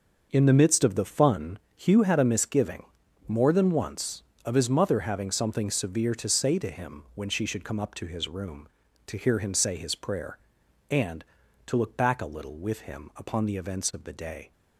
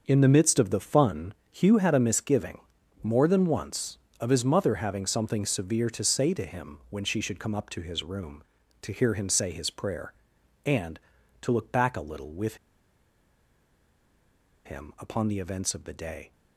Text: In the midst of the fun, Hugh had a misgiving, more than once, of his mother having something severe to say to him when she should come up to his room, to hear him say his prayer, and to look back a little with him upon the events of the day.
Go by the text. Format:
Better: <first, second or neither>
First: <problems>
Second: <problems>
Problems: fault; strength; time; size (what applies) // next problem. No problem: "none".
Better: first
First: starts louder than the rest; noticeable; until 1.3 s; 6 dB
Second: starts louder than the rest; noticeable; until 1.0 s; 6 dB // pauses between "with" and "him"; strong; at 12.5 s; 2.0 s long